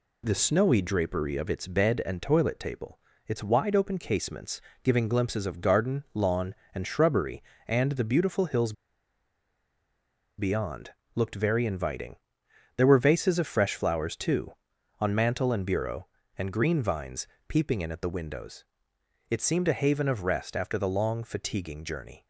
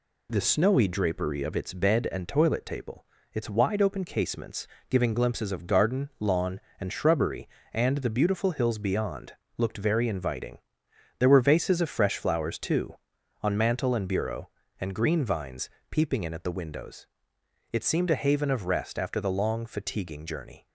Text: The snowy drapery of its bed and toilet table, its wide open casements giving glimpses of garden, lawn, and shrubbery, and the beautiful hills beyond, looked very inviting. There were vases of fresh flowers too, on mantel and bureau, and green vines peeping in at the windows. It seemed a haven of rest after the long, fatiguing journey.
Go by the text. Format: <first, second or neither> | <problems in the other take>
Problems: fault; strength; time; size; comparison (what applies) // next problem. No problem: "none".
second | pauses between "casements" and "giving"; slight; at 4.5 s; 0.24 s long; slight in the second // pauses between "hills" and "beyond"; strong; at 8.7 s; 1.6 s long // pauses between "vines" and "peeping"; slight; at 17.2 s; 0.22 s long; slight in the second